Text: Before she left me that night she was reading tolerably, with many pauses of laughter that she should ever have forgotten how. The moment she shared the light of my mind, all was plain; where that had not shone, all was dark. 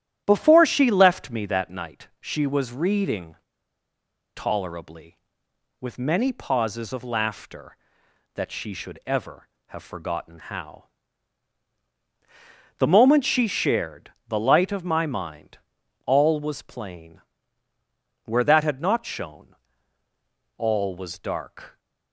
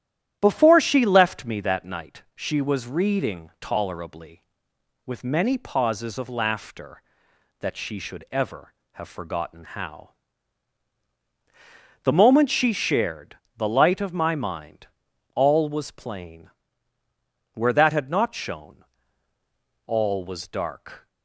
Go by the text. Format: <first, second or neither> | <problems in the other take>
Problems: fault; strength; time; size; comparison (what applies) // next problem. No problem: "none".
second | starts louder than the rest; strong; until 1.2 s; 11.5 dB; strong in the second // pauses between "reading" and "tolerably"; at 3.3 s; 0.99 s long // pauses between "shared" and "the"; slight; at 14.0 s; 0.20 s long; slight in the second